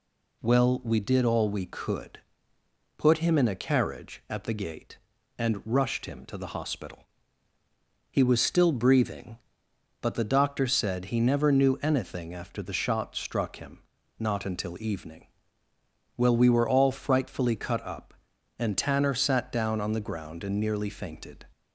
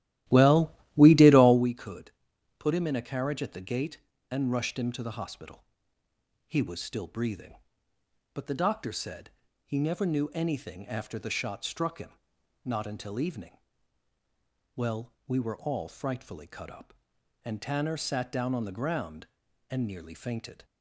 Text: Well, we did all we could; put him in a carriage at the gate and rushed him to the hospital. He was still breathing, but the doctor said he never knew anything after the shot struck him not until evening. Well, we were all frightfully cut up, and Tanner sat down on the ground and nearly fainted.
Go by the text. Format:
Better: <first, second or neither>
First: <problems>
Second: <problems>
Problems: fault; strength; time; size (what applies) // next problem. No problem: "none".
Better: first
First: pauses between "him" and "not"; at 13.7 s; 0.38 s long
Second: starts louder than the rest; strong; until 1.7 s; 14.5 dB // pauses between "said" and "he"; slight; at 9.3 s; 0.34 s long // pauses between "him" and "not"; noticeable; at 12.1 s; 0.54 s long